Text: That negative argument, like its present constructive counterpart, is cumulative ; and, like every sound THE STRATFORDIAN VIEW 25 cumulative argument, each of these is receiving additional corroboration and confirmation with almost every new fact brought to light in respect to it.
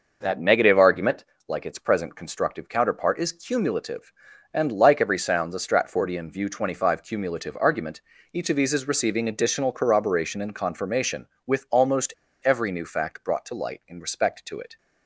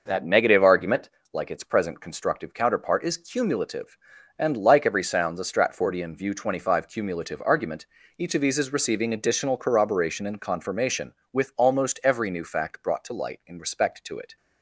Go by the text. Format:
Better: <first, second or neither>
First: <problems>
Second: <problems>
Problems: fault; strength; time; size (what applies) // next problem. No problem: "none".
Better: second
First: pauses between "almost" and "every"; slight; at 12.1 s; 0.29 s long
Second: none